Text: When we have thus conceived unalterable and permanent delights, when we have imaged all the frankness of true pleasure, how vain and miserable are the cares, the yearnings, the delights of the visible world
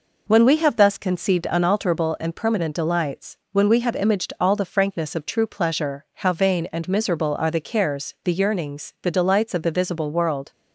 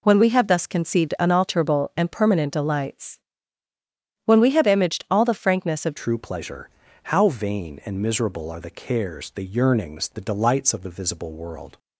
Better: first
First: none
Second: changes voice at "true"; from 5.9 s on; 5.8 s long

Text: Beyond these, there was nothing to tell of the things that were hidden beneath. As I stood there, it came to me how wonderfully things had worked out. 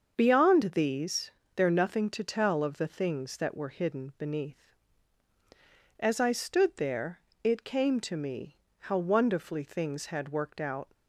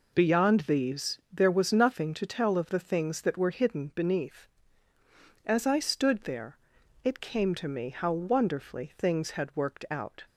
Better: second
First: starts louder than the rest; until 1.1 s; 6.5 dB // skips "was"; at 1.6 s // pauses between "me" and "how"; slight; at 8.5 s; 0.24 s long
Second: none

